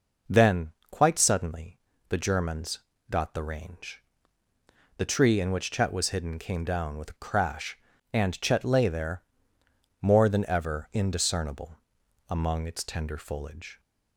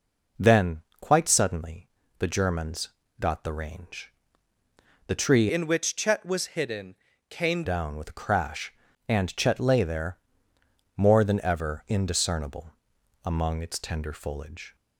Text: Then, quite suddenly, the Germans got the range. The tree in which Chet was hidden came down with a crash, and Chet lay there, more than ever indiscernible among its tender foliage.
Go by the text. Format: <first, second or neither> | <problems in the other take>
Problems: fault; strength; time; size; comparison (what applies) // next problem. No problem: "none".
first | pauses between "Germans" and "got"; slight; at 2.8 s; 0.30 s long; slight in the first // changes voice from "in" to "came"; from 5.5 to 7.6 s; 2.1 s long // pauses between "hidden" and "came"; slight; at 6.9 s; 0.34 s long // pauses between "indiscernible" and "among"; noticeable; at 12.7 s; 0.52 s long; noticeable in the first